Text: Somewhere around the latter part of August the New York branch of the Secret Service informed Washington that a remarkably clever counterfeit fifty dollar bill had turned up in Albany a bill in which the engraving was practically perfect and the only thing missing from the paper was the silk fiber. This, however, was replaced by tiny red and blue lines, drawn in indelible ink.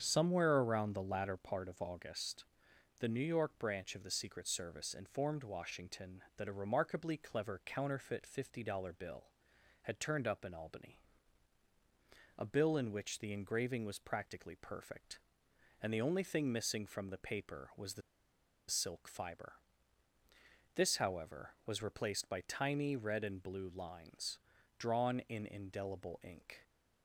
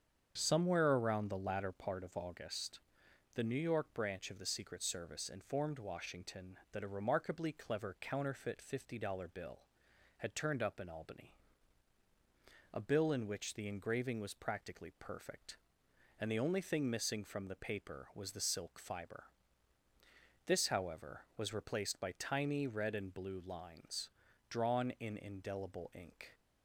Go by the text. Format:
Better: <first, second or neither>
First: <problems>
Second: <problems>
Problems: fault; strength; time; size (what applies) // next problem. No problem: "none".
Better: second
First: starts louder than the rest; strong; until 1.0 s; 7.5 dB // pauses between "August" and "the"; noticeable; at 2.4 s; 0.56 s long // pauses between "Albany" and "a"; strong; at 10.9 s; 1.4 s long // pauses between "the" and "silk"; noticeable; at 18.0 s; 0.68 s long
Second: starts louder than the rest; strong; until 1.3 s; 7.5 dB // pauses between "August" and "the"; noticeable; at 2.8 s; 0.56 s long // pauses between "Albany" and "a"; strong; at 11.3 s; 1.4 s long